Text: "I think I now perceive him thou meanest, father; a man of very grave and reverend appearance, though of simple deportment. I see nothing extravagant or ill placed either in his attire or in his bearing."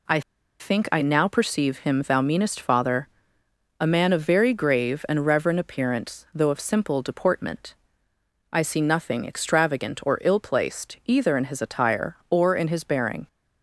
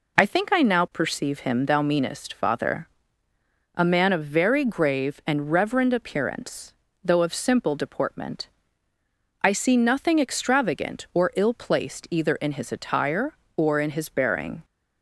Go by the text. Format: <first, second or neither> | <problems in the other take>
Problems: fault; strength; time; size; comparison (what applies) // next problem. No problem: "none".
second | pauses between "I" and "think"; at 0.2 s; 0.39 s long